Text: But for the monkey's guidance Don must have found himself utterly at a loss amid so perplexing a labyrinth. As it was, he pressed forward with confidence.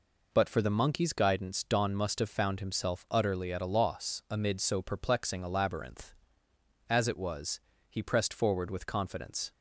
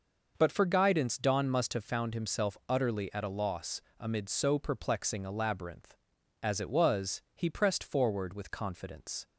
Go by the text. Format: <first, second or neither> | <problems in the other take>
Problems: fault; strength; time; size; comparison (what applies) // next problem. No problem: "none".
first | skips "the monkey's"; at 0.6 s // pauses between "loss" and "amid"; slight; at 3.8 s; 0.18 s long